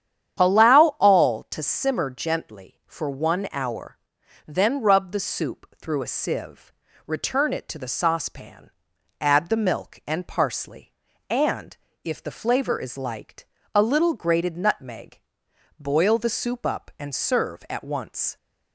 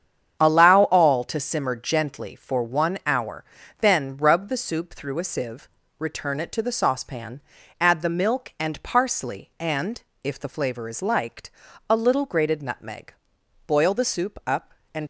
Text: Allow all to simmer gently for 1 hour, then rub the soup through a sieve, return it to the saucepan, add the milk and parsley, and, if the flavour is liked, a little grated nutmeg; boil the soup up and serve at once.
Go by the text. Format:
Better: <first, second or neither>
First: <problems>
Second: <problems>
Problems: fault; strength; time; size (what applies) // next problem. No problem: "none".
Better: first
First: starts louder than the rest; strong; until 1.5 s; 9.5 dB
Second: starts louder than the rest; strong; until 1.4 s; 8 dB // stops before "serve at once"; at 15.0 s